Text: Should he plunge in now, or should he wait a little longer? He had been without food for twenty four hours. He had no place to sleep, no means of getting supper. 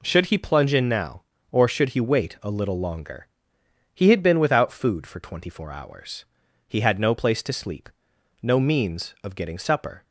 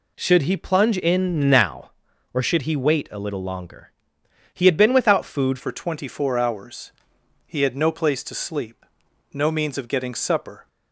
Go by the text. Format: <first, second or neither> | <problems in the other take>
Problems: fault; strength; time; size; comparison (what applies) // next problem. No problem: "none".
first | changes voice at "for"; from 5.5 s on; 5.1 s long